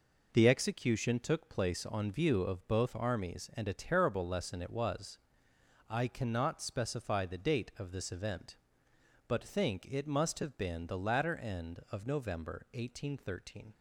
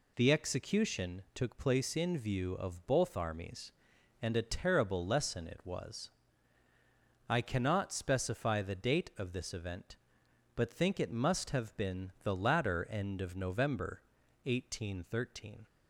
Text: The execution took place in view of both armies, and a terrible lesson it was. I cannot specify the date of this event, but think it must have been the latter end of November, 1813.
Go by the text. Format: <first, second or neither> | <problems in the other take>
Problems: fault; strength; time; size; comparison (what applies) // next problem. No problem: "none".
second | says "on" for "in"; at 1.8 s